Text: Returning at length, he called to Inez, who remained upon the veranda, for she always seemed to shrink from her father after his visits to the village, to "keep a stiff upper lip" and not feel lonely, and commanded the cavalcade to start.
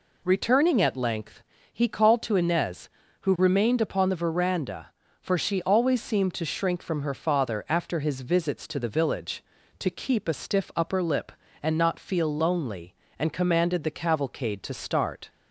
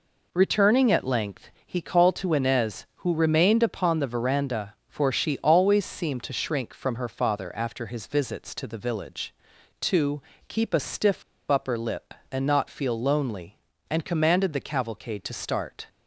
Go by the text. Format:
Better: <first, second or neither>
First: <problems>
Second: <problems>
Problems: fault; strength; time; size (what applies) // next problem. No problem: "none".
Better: first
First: none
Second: pauses between "to" and "keep"; slight; at 10.2 s; 0.24 s long // pauses between "stiff" and "upper"; slight; at 11.2 s; 0.27 s long